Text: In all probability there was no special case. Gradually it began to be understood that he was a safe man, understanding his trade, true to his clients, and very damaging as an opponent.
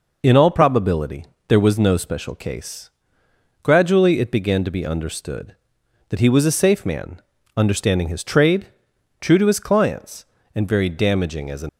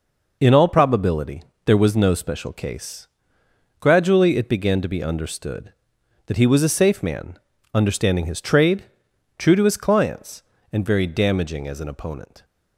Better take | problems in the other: second | pauses between "probability" and "there"; slight; at 1.2 s; 0.22 s long; slight in the second // stops before "opponent"; at 11.6 s

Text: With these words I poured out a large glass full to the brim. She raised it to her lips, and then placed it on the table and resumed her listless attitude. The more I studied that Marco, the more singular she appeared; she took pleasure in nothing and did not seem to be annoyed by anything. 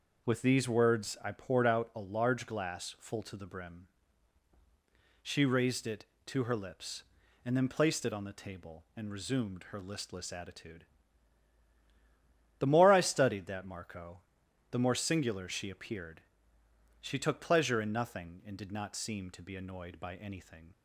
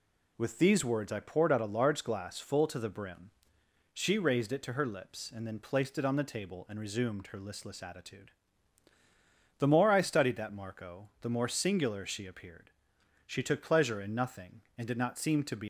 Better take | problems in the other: first | stops before "annoyed by anything"; at 15.6 s

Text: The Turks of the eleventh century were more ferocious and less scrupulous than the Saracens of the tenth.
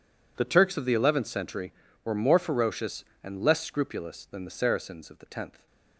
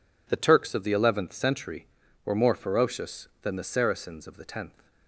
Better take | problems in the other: first | skips "and less scrupulous"; at 3.3 s

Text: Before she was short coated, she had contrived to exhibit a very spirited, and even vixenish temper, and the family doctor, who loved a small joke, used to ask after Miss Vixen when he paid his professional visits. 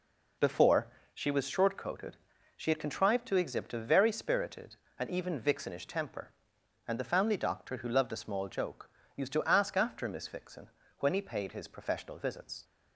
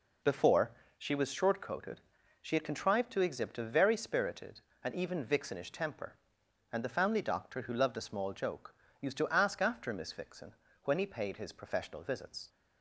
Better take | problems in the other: neither | pauses between "Before" and "she"; slight; the same in both // pauses between "Vixen" and "when"; slight; the same in both

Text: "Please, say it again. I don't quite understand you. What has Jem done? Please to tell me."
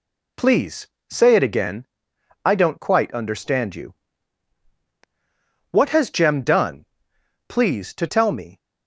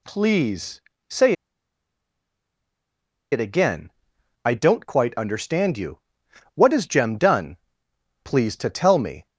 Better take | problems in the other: first | pauses between "say" and "it"; strong; at 1.3 s; 1.9 s long

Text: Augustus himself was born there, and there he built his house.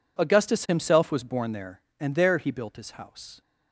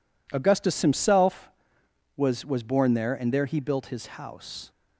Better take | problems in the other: first | says "was" twice; at 2.4 s

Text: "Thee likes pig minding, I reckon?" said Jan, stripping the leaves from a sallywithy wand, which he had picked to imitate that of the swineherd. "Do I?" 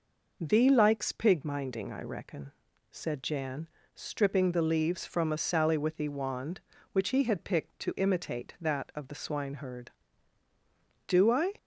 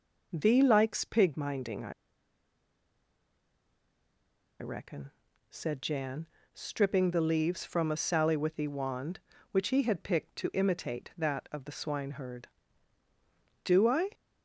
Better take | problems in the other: first | pauses between "I" and "reckon"; strong; at 1.9 s; 2.6 s long

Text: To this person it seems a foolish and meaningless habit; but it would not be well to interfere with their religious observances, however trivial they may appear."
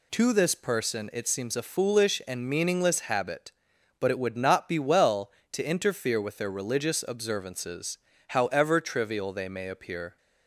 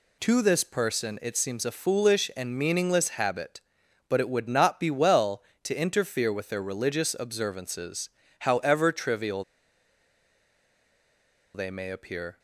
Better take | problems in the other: first | pauses between "trivial" and "they"; strong; at 9.4 s; 2.1 s long

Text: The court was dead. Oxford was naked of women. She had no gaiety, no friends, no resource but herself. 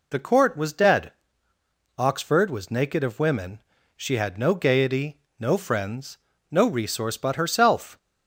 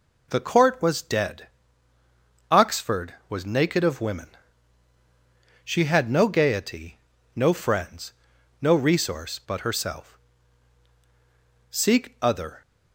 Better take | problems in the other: first | goes on to say "Seek other"; noticeable; from 11.7 s on; 0.90 s long

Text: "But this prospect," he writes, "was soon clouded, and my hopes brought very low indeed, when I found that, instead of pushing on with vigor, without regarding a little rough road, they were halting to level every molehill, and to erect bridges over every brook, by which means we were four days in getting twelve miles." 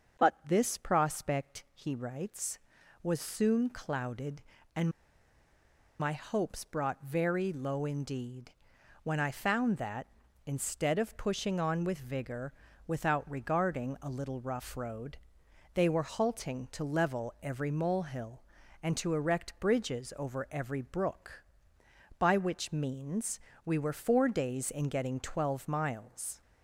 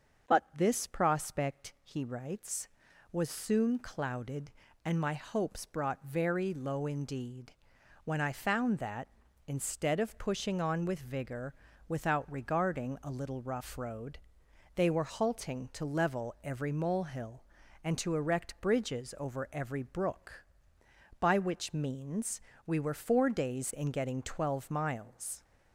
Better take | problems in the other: second | starts louder than the rest; until 1.2 s; 6.5 dB; also in the second // pauses between "and" and "my"; at 4.8 s; 1.1 s long // pauses between "means" and "we"; slight; at 23.3 s; 0.26 s long; slight in the second

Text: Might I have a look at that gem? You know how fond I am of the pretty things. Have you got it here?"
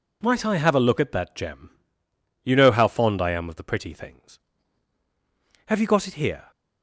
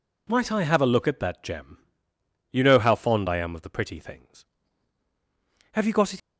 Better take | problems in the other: first | stops before "here"; at 6.1 s

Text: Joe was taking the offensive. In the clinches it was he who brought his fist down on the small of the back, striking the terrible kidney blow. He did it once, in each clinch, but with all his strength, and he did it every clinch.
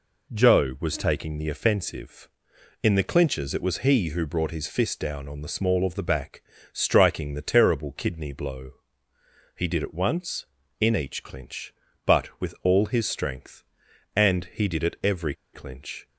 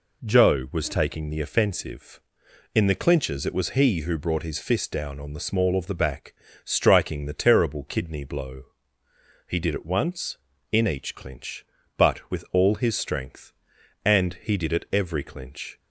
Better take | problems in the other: second | pauses between "every" and "clinch"; slight; at 15.3 s; 0.19 s long

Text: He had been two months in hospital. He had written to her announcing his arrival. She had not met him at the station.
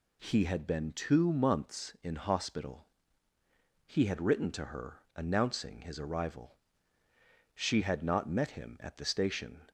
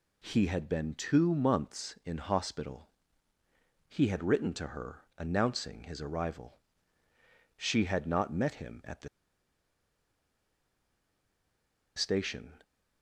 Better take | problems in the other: first | pauses between "her" and "announcing"; slight; at 5.0 s; 0.16 s long; slight in the first // pauses between "the" and "station"; strong; at 9.0 s; 2.8 s long

